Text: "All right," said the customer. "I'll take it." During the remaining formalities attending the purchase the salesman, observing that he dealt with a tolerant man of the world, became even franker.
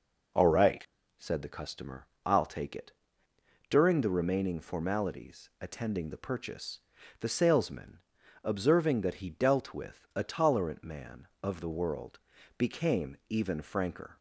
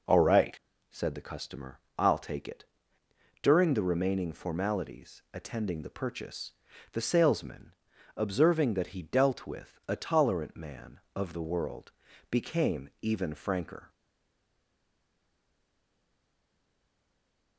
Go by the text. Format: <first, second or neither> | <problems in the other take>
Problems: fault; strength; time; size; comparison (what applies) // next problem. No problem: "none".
first | pauses between "purchase" and "the"; at 6.5 s; 0.40 s long; also in the first // stays silent after the last word; strong; from 13.9 s on; 3.6 s long